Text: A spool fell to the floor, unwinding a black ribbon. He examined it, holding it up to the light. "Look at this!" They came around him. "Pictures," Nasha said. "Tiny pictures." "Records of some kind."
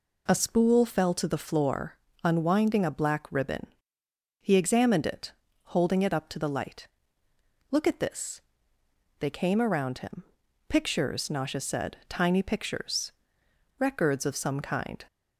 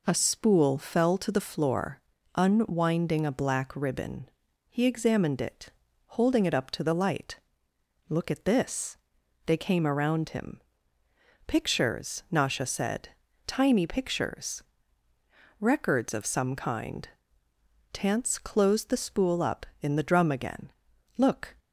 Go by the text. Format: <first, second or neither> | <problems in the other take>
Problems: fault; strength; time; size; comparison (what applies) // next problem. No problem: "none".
first | goes on to say "Tance closed the spool up in the drum again Look"; strong; from 17.9 s on; 3.6 s long